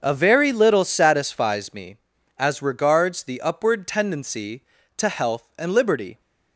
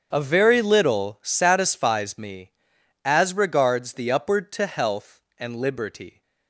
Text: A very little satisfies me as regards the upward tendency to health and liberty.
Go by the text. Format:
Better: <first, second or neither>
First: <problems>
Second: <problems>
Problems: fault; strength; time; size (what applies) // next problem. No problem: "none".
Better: first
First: starts louder than the rest; until 1.0 s; 6.5 dB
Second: starts louder than the rest; strong; until 1.1 s; 7.5 dB // skips "tendency"; at 4.5 s